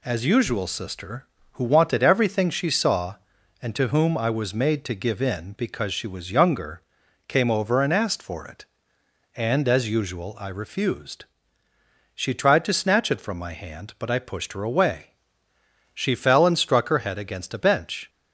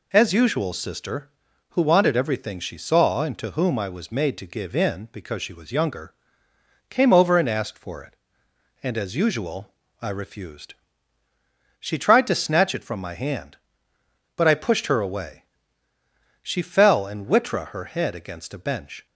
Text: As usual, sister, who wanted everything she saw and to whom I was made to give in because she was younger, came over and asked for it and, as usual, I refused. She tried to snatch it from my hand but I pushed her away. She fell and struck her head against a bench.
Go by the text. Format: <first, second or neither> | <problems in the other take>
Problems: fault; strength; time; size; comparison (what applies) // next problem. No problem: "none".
first | says "witra" for "struck"; at 17.2 s